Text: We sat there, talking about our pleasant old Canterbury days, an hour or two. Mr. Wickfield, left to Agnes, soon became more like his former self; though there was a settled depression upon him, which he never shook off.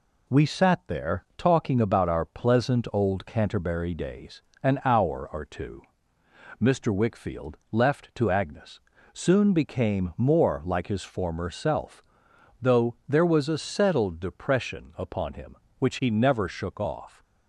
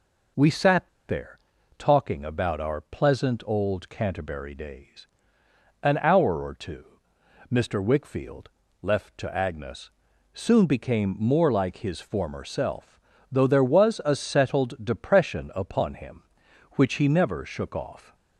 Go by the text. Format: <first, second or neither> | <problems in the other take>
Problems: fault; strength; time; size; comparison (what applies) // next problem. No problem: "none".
first | pauses between "sat" and "there"; slight; at 0.8 s; 0.19 s long